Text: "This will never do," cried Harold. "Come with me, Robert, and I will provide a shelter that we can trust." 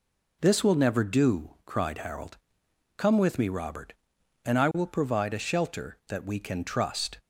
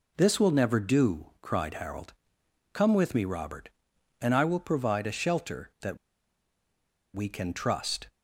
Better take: first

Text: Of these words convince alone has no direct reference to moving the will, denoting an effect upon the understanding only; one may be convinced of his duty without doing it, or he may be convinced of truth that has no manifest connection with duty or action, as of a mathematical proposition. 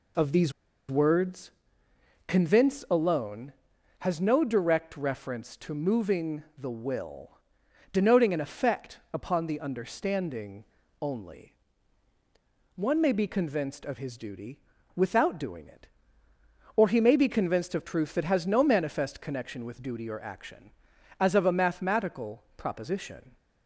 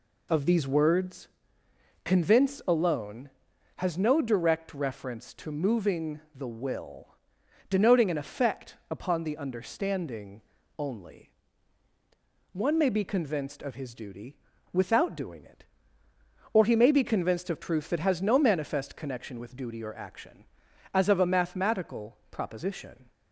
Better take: second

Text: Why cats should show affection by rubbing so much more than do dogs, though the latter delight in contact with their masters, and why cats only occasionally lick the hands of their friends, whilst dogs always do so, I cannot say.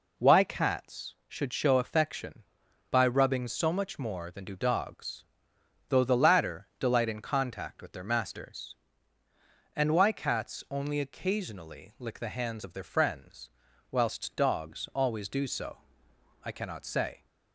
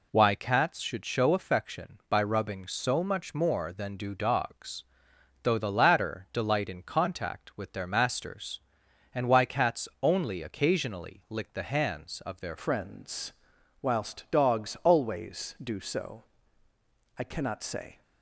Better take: first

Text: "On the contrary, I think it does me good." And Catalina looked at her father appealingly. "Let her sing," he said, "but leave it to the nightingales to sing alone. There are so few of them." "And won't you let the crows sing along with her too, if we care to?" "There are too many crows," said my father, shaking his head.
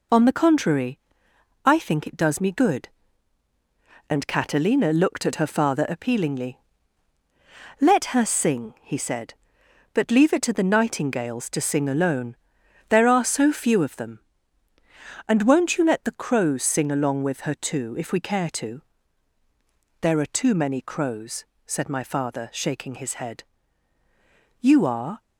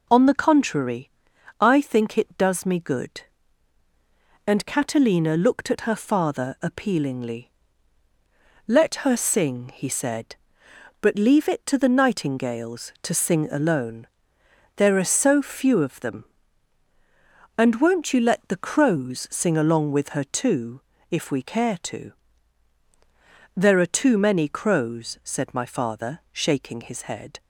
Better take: second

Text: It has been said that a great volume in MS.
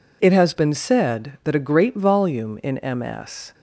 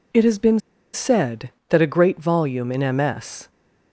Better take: first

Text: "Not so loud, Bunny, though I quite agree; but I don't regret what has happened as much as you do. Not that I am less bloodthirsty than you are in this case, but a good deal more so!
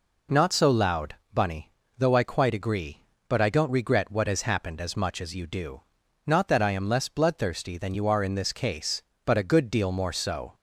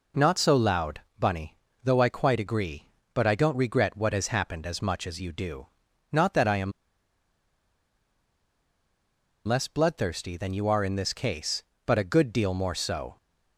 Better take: first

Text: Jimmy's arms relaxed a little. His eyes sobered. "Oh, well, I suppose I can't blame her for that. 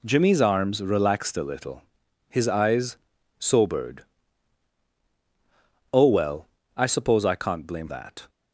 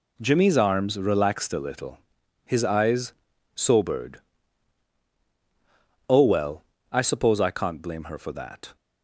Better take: second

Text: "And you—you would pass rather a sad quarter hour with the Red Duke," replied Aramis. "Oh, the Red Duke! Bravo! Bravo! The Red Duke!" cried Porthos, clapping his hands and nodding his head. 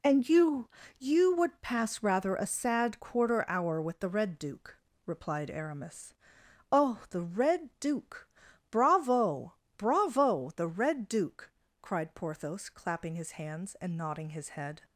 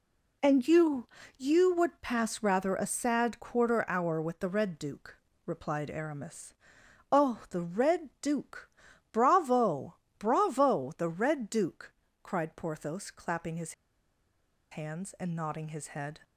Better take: first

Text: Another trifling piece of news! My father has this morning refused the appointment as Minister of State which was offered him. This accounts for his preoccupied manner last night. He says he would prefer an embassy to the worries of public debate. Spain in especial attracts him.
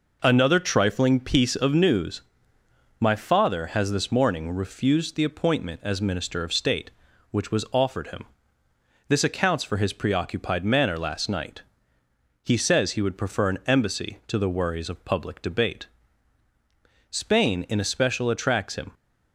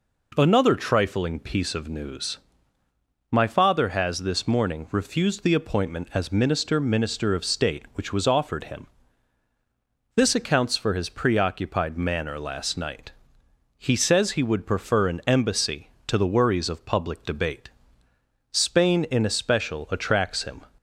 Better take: first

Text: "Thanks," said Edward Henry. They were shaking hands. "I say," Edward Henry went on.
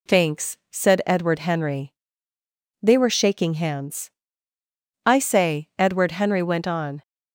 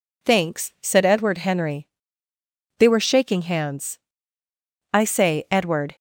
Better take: first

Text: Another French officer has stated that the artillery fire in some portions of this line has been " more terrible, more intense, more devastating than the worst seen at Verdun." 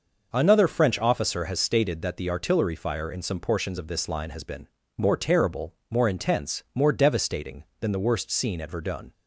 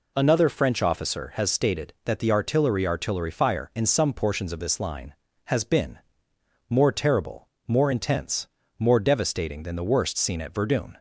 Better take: first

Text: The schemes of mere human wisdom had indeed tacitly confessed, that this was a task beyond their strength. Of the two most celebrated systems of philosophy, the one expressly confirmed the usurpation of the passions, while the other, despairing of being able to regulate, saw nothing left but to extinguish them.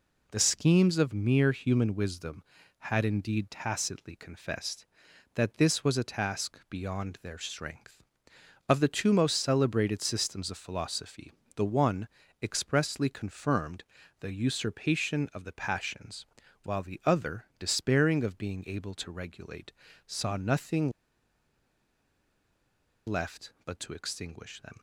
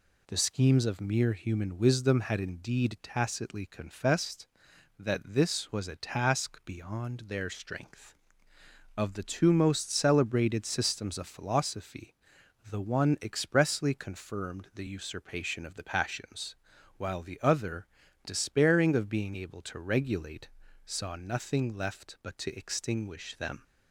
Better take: second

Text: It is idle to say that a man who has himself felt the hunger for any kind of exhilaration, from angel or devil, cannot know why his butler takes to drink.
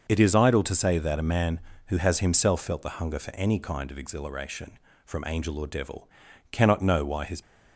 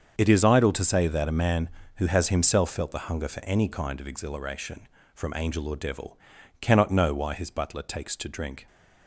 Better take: second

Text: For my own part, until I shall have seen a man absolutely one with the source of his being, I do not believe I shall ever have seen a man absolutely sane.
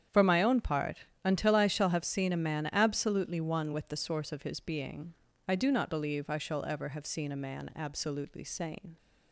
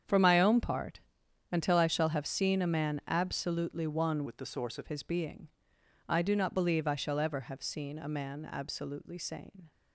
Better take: first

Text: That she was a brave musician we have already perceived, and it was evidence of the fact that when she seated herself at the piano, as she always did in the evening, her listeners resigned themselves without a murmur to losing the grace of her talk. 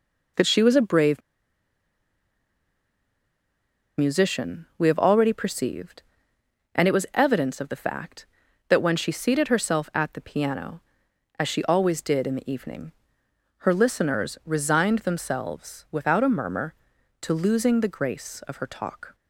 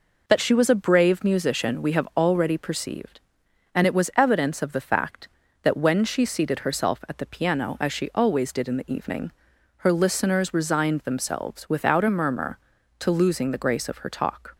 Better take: second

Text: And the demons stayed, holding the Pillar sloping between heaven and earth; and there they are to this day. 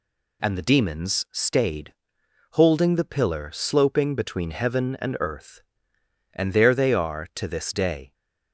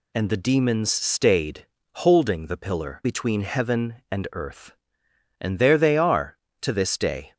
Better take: first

